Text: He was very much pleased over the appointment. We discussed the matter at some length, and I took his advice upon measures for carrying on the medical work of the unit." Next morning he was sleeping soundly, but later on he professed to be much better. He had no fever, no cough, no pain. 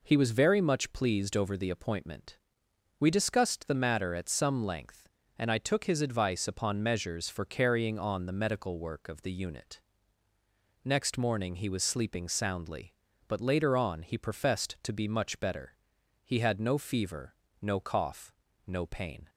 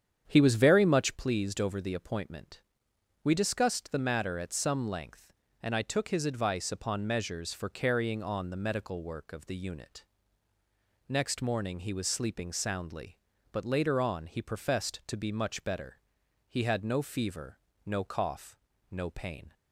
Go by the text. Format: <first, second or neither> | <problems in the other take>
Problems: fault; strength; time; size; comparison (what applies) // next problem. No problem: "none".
first | starts louder than the rest; strong; until 1.2 s; 8.5 dB